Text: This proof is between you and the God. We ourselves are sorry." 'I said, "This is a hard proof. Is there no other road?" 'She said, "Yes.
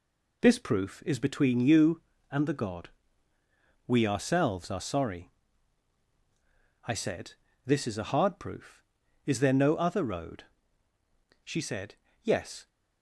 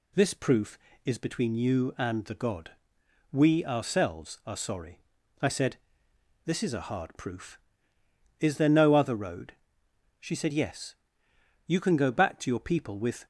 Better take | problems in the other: first | goes on to say "You can go back to your people with"; from 11.6 s on; 1.6 s long

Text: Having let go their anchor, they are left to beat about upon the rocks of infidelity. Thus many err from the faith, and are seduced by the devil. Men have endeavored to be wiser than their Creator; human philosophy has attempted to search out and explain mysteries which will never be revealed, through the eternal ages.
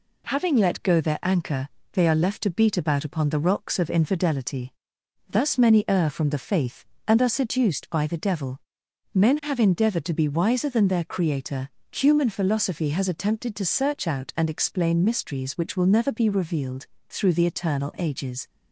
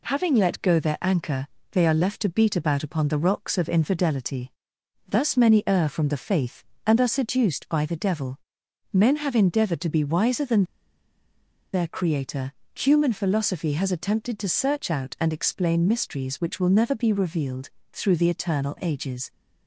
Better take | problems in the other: first | pauses between "than" and "their"; at 10.6 s; 1.0 s long

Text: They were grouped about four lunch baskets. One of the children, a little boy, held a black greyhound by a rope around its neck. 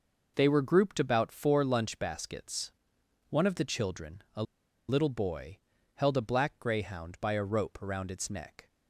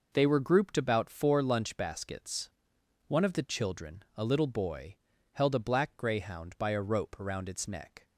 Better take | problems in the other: second | pauses between "a" and "little"; at 4.4 s; 0.45 s long

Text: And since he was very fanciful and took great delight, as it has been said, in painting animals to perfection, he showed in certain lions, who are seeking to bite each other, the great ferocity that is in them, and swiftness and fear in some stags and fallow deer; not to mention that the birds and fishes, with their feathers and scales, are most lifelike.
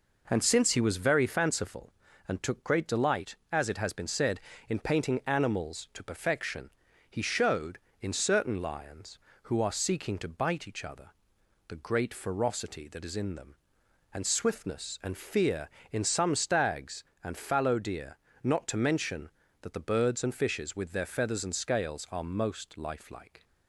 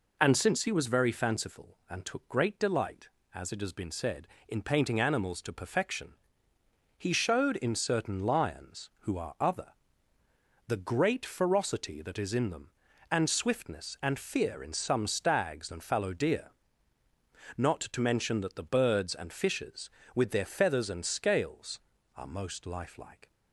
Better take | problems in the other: first | skips "seeking to bite each"; at 9.3 s

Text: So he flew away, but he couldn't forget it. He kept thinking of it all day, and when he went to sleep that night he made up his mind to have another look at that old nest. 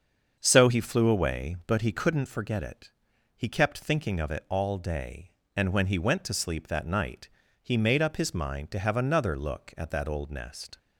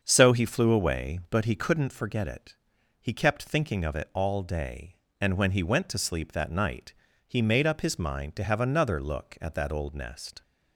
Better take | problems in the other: neither | starts louder than the rest; the same in both // pauses between "night" and "he"; slight; the same in both

